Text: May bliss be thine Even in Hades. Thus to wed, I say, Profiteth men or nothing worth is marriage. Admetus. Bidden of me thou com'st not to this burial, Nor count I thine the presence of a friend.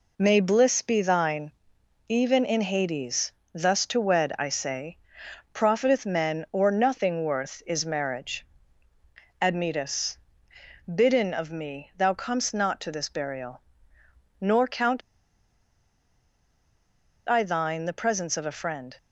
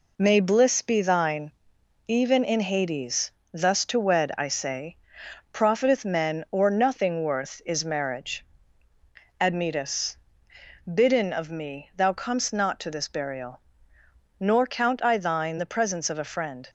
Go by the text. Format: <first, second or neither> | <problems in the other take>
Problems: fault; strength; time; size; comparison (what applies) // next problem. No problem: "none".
second | pauses between "thine" and "Even"; noticeable; at 1.5 s; 0.56 s long; noticeable in the second // pauses between "count" and "I"; strong; at 15.0 s; 2.2 s long